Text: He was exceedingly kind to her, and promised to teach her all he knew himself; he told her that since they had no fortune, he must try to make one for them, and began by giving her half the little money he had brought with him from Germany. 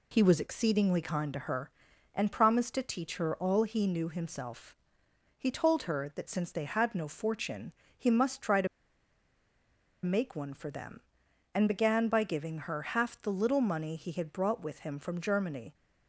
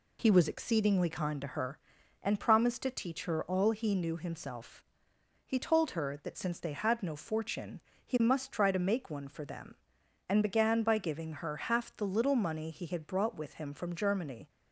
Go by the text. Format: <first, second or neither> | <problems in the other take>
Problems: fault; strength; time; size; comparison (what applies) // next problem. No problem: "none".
second | pauses between "to" and "make"; strong; at 8.6 s; 1.3 s long